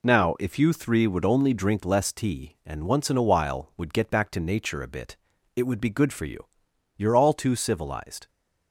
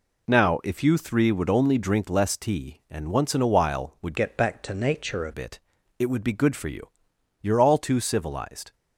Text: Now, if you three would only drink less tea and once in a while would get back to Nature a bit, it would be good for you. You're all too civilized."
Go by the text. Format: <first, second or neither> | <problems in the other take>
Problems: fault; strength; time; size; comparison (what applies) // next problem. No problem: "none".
first | changes voice from "get" to "a"; from 4.1 to 5.3 s; 1.2 s long